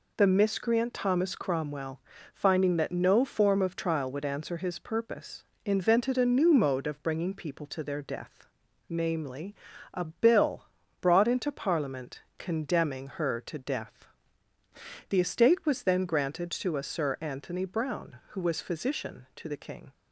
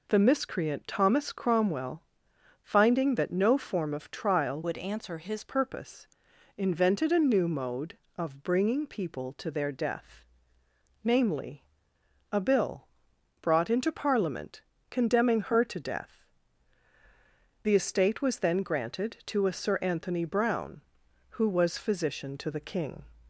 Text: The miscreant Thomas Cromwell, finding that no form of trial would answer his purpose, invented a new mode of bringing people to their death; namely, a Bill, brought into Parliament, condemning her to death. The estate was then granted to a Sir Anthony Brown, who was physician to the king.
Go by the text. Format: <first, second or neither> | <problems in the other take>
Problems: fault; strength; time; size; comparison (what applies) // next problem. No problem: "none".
first | changes voice from "would" to "his"; from 4.6 to 5.4 s; 0.8 s long